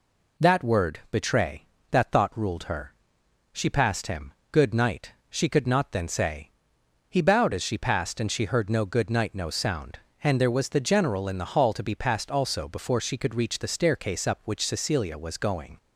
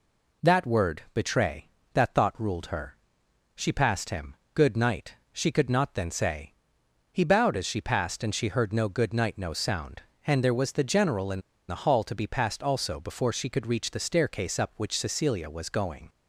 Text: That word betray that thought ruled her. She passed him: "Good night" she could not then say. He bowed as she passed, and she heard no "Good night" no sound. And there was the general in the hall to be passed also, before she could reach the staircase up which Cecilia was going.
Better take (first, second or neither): first